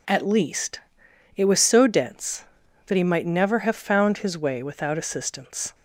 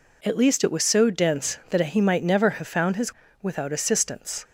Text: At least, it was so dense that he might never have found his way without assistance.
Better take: first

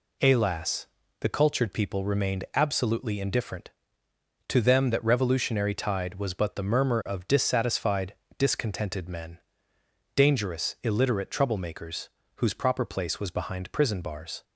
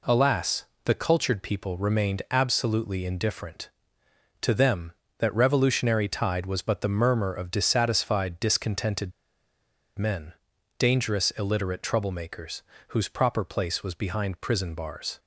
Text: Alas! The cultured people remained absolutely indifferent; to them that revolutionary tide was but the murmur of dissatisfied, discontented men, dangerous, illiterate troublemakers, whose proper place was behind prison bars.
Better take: first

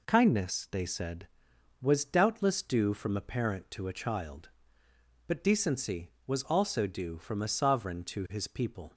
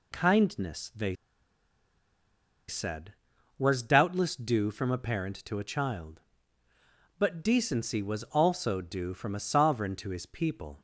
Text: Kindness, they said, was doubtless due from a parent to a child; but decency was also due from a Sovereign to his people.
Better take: first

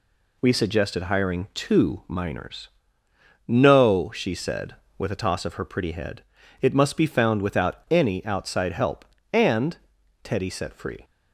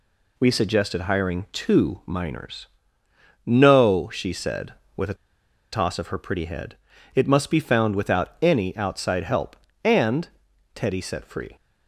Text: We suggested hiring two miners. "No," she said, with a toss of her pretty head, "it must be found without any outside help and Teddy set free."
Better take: first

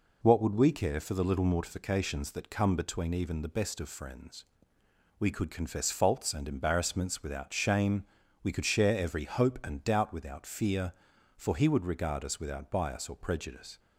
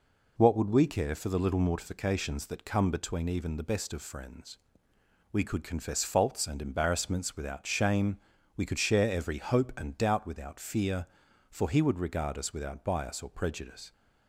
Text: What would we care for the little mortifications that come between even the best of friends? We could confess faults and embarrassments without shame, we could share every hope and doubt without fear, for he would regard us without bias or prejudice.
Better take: neither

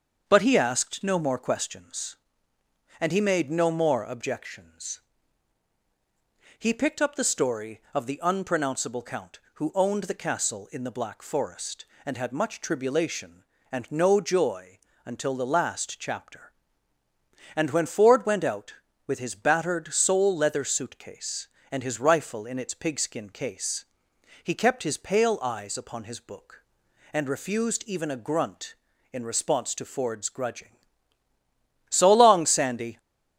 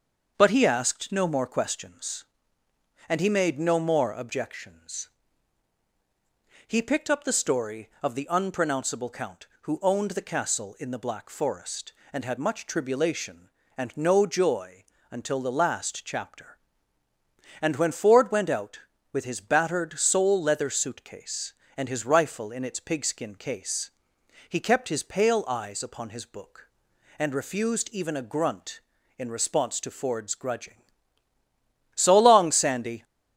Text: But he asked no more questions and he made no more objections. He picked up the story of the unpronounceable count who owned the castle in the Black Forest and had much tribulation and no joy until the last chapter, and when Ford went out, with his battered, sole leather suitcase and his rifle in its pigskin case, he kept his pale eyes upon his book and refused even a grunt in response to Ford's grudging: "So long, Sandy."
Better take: neither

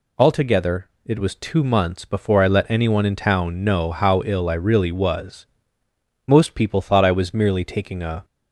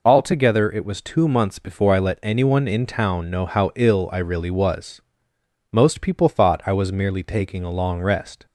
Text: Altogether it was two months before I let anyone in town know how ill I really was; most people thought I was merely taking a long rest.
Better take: second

